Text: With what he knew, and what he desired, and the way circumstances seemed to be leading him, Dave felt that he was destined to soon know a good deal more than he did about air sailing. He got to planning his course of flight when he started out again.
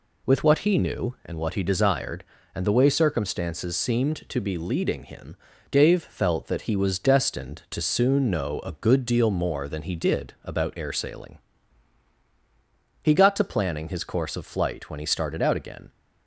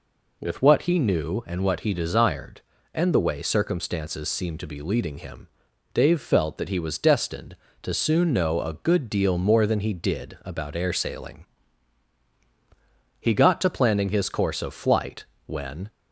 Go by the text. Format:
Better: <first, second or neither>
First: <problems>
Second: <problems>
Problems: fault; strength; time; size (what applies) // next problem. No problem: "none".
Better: first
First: none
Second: pauses between "flight" and "when"; slight; at 15.2 s; 0.22 s long // stops before "he started out again"; at 15.9 s